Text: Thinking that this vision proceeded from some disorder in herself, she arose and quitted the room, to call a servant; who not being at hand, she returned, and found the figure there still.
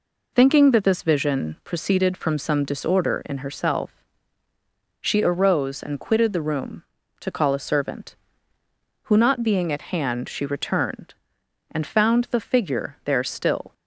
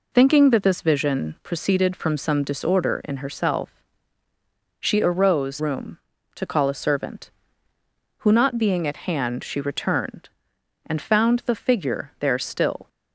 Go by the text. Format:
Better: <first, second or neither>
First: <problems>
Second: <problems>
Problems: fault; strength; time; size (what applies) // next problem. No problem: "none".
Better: first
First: none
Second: skips "and quitted the"; at 5.5 s